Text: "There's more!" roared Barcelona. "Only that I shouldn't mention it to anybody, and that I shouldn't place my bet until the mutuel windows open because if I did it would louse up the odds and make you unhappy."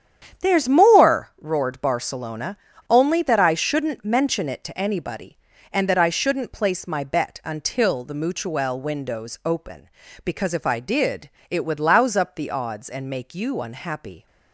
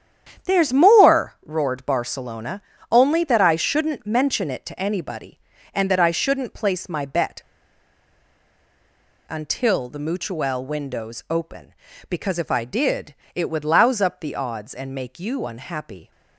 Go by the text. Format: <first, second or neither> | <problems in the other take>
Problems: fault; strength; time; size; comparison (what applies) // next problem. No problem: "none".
first | starts louder than the rest; strong; until 1.5 s; 9 dB; strong in the first // pauses between "bet" and "until"; strong; at 7.4 s; 1.8 s long // pauses between "did" and "it"; slight; at 13.1 s; 0.22 s long; slight in the first